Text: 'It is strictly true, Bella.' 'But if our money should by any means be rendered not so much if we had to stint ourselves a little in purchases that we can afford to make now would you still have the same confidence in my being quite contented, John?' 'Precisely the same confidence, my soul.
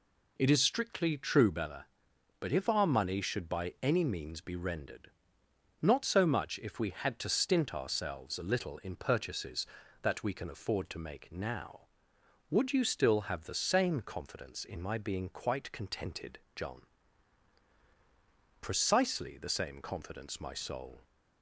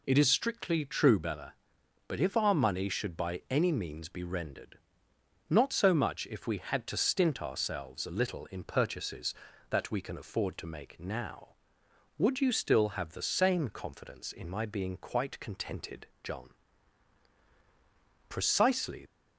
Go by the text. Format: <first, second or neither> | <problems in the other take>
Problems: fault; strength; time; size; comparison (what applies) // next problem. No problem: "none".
first | pauses between "rendered" and "not"; noticeable; at 4.7 s; 0.70 s long; noticeable in the first // stops before "the same confidence my soul"; at 19.0 s